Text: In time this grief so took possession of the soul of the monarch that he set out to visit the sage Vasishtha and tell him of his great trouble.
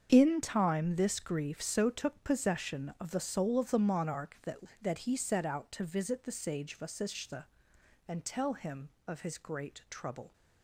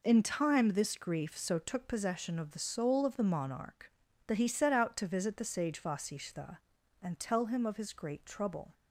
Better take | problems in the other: second | starts louder than the rest; strong; until 1.1 s; 7 dB // says "that" twice; at 4.8 s

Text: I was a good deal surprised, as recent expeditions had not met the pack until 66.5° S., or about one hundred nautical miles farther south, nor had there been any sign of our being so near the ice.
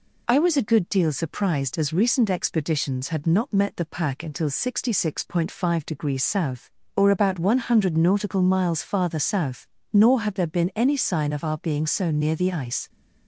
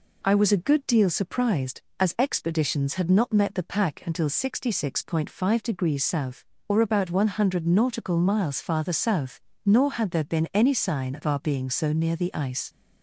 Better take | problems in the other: first | skips "recent"; at 2.1 s

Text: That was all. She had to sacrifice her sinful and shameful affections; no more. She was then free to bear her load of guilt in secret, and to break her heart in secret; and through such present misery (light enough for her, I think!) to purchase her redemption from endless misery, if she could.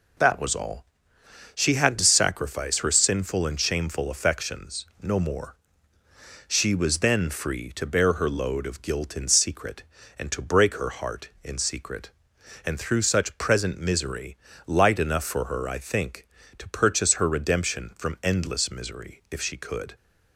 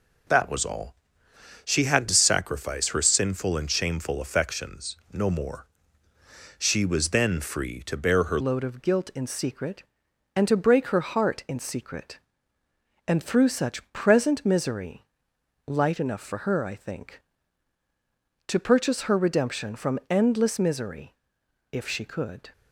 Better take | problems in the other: first | changes voice at "load"; from 8.4 s on; 14.1 s long

